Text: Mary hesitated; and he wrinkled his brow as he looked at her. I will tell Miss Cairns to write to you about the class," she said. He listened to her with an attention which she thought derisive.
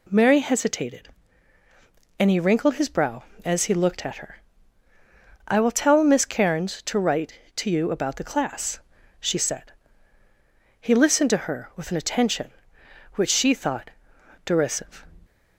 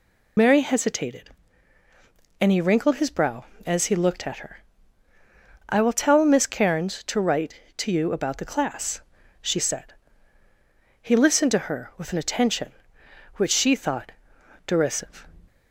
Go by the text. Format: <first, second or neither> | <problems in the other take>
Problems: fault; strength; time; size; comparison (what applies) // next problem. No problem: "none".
first | loses the start of "Mary"; at 0.3 s; 90 ms // pauses between "thought" and "derisive"; noticeable; at 14.1 s; 0.56 s long; noticeable in the first